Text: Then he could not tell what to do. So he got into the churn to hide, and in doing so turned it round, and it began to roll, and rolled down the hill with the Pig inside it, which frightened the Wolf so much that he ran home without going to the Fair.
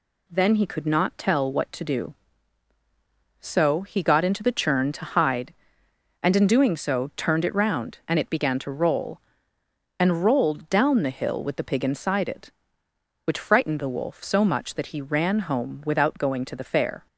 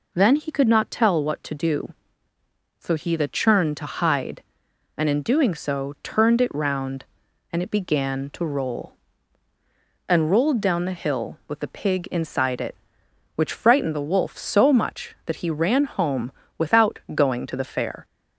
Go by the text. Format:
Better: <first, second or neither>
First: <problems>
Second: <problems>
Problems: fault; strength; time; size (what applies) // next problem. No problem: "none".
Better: first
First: none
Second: skips "got into"; at 3.1 s // pauses between "home" and "without"; slight; at 16.3 s; 0.28 s long // pauses between "without" and "going"; slight; at 16.9 s; 0.16 s long